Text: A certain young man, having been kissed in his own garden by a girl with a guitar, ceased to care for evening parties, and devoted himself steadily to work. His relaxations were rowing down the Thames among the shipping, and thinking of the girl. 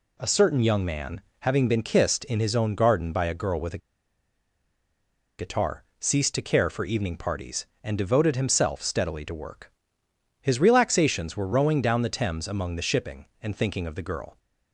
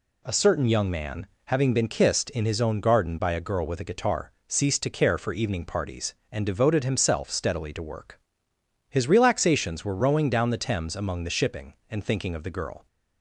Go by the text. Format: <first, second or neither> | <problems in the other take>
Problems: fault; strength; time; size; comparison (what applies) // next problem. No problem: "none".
second | pauses between "a" and "guitar"; strong; at 3.7 s; 1.6 s long